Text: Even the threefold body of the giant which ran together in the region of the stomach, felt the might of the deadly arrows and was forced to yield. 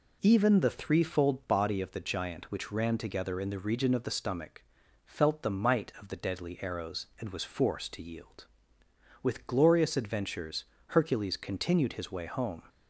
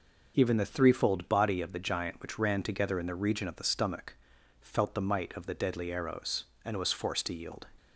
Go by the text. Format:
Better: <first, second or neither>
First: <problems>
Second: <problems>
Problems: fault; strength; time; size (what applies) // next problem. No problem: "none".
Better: second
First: goes on to say "With glorious adventures Hercules continued his way home"; strong; from 9.2 s on; 3.4 s long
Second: none